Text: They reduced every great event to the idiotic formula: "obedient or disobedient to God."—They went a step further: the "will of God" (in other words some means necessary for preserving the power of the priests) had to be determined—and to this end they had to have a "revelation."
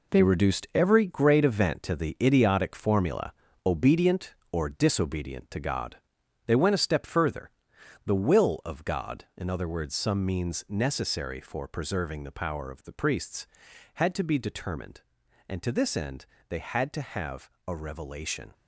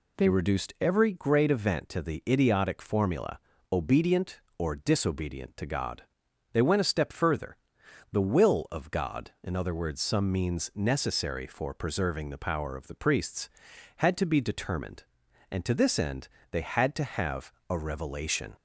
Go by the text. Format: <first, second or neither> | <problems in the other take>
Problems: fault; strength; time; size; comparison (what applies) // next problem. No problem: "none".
second | gets quieter; strong; throughout; 8.5 dB // pauses between "end" and "they"; slight; at 16.2 s; 0.22 s long; slight in the second // pauses between "have" and "a"; slight; at 17.4 s; 0.18 s long; slight in the second